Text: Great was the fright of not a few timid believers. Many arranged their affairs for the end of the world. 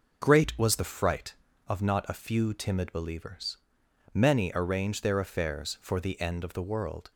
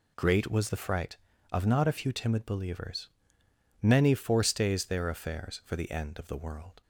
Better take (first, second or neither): first